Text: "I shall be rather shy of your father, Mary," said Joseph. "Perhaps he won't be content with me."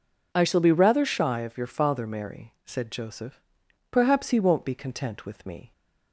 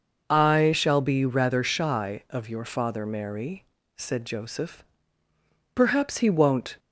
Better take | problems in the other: first | stops before "be content with me"; at 6.7 s

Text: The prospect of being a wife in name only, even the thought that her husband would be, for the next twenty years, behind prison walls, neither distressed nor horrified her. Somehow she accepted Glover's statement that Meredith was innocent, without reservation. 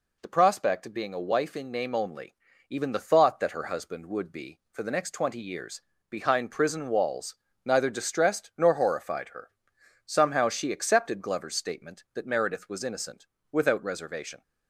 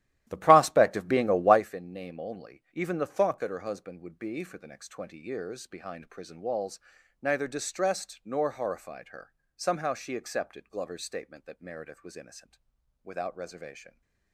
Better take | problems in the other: first | starts louder than the rest; strong; until 1.7 s; 13.5 dB

